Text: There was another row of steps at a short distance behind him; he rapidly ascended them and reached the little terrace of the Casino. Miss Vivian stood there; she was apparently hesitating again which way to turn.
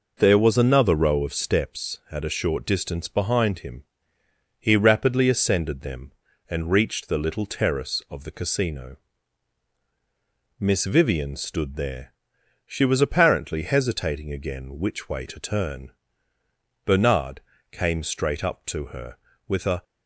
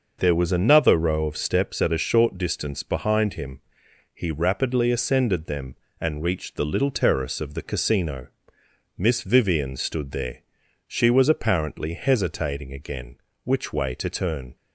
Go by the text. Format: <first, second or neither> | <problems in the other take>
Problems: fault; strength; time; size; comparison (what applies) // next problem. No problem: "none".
second | goes on to say "Bernard came straight up to her with a"; strong; from 16.8 s on; 2.9 s long